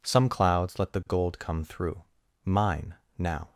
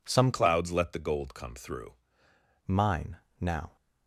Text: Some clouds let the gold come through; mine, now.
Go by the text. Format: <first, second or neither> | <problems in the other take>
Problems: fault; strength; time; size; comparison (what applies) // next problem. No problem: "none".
first | changes voice from "clouds" to "through"; from 0.3 to 1.9 s; 1.6 s long